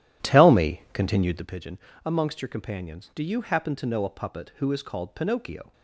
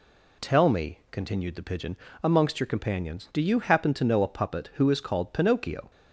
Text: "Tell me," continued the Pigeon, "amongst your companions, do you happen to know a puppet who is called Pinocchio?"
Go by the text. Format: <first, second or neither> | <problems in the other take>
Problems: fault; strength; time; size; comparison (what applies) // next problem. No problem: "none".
second | starts louder than the rest; strong; until 1.6 s; 12 dB